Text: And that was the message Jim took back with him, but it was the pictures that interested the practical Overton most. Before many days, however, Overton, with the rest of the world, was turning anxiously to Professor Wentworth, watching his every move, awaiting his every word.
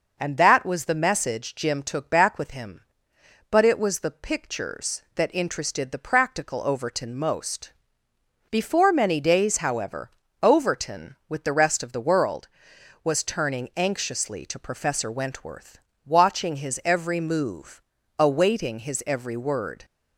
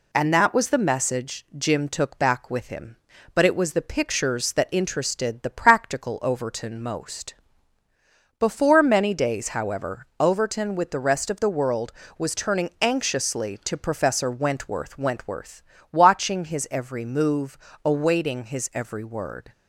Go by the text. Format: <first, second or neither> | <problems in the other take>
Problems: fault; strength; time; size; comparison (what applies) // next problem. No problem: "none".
first | says "Wentworth" twice; at 14.9 s